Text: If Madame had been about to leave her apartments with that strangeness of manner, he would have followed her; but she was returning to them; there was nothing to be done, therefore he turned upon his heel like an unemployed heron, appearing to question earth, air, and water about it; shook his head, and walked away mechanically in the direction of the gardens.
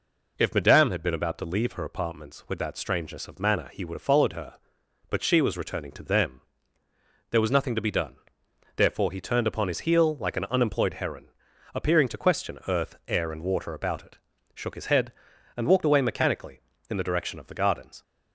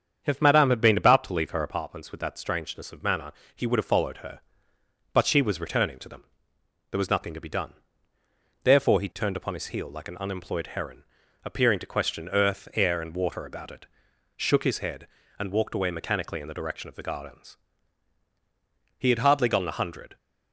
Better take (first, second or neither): first